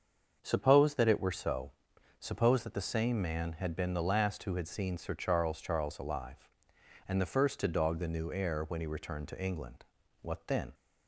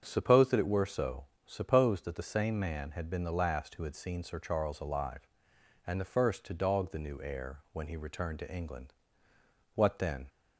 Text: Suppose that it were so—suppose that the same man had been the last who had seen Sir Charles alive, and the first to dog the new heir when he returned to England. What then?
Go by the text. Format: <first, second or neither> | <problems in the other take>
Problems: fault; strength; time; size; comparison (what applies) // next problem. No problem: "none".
second | starts louder than the rest; until 1.4 s; 6.5 dB; strong in the second // says "Charles" twice; at 5.5 s